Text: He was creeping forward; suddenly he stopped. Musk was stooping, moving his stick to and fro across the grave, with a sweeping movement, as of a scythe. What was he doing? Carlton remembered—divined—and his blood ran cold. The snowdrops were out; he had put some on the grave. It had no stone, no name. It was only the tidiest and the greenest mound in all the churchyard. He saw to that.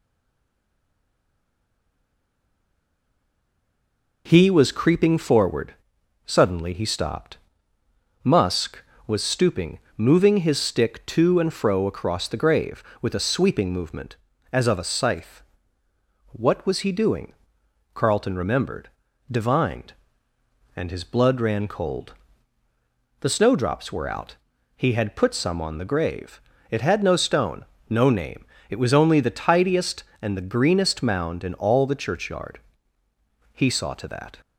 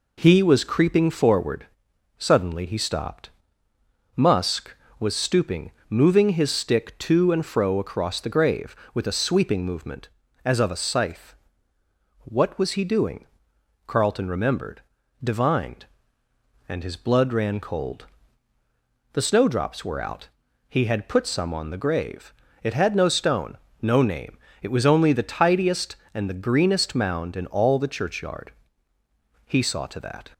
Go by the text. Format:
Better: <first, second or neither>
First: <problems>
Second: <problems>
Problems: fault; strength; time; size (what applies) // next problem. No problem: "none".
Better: second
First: stays silent before the first word; strong; until 4.2 s; 4.2 s long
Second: none